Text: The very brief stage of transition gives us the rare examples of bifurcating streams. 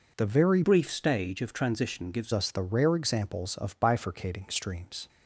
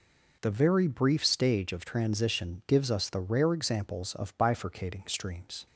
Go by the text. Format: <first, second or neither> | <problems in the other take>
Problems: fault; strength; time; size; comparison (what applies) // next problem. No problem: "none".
second | changes voice from "brief" to "gives"; from 0.6 to 2.3 s; 1.7 s long